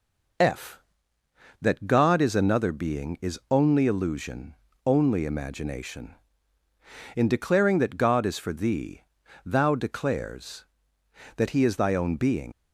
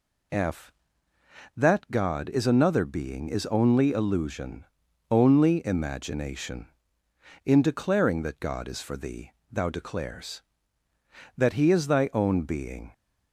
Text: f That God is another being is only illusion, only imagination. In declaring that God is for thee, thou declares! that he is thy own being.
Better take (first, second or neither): second